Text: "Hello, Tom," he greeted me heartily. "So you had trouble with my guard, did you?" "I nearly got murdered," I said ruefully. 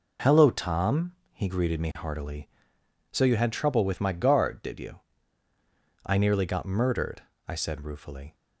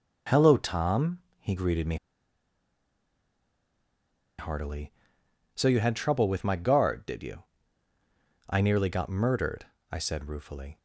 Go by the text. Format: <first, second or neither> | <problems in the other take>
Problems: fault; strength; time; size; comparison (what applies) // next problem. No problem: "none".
first | pauses between "me" and "heartily"; strong; at 1.9 s; 2.4 s long